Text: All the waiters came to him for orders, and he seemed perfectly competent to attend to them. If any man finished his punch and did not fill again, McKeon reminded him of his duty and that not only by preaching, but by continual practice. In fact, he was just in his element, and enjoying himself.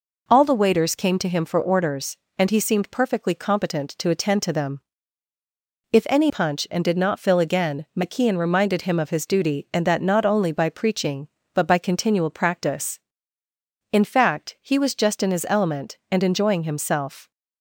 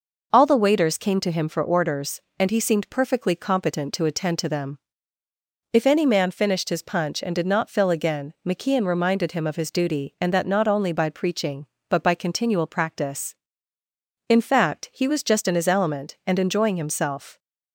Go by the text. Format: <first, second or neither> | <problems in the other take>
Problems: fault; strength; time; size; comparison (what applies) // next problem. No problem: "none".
second | skips "man finished his"; at 6.2 s